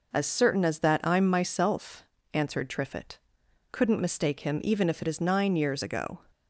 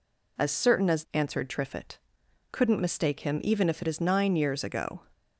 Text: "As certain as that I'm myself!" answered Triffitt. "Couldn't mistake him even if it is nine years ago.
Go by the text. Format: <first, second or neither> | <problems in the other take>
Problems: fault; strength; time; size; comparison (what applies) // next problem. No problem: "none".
first | skips "that I'm myself"; at 1.0 s